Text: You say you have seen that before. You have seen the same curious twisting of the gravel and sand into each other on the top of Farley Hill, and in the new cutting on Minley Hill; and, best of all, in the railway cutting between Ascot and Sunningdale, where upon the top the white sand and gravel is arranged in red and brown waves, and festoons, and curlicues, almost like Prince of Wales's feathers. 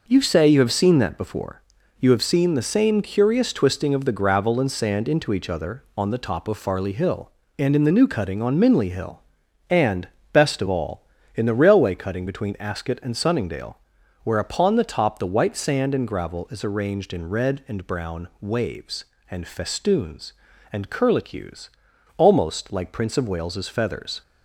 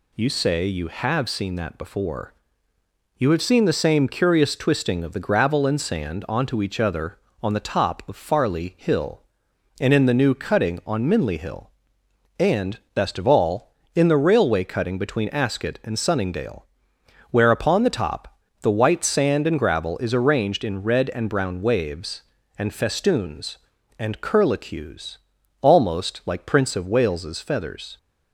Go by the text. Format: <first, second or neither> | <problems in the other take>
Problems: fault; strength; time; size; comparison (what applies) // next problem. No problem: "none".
first | says "onto" for "into"; at 6.2 s // pauses between "top" and "the"; slight; at 18.3 s; 0.24 s long